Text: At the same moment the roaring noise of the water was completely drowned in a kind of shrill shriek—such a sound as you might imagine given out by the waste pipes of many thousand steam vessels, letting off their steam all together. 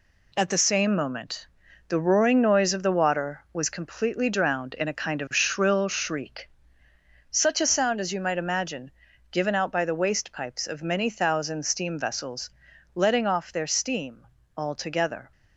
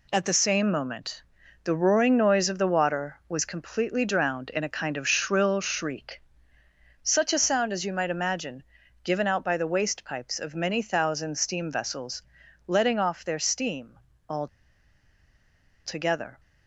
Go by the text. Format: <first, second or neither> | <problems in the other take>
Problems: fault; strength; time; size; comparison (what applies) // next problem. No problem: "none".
first | pauses between "moment" and "the"; at 1.2 s; 0.44 s long; also in the first // pauses between "imagine" and "given"; at 8.6 s; 0.40 s long; also in the first // pauses between "steam" and "all"; slight; at 13.9 s; 0.32 s long; slight in the first // pauses between "all" and "together"; strong; at 14.4 s; 1.3 s long